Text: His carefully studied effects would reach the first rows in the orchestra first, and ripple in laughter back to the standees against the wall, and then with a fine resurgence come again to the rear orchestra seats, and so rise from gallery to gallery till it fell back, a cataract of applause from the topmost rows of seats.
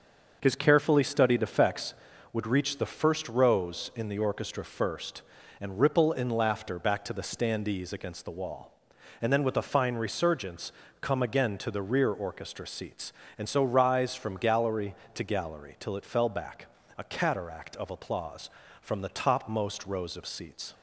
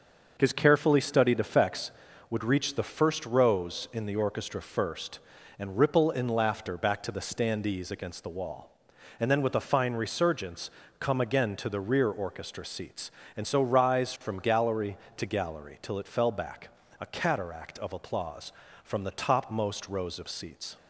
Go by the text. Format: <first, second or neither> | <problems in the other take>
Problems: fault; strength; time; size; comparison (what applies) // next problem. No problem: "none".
neither | starts louder than the rest; the same in both // pauses between "resurgence" and "come"; slight; the same in both